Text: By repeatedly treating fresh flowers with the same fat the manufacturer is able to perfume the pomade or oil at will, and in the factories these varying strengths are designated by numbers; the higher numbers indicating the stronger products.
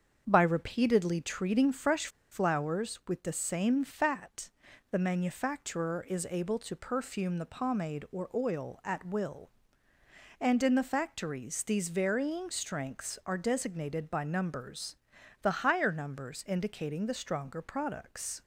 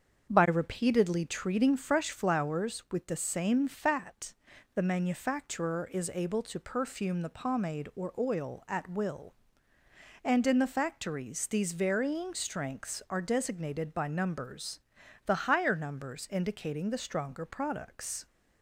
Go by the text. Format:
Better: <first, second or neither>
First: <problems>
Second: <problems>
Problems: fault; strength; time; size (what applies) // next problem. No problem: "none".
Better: second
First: starts louder than the rest; until 1.2 s; 7 dB // pauses between "fresh" and "flowers"; slight; at 2.0 s; 0.23 s long // pauses between "fat" and "the"; at 4.4 s; 0.44 s long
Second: starts louder than the rest; until 1.3 s; 7 dB // pauses between "fat" and "the"; at 4.3 s; 0.44 s long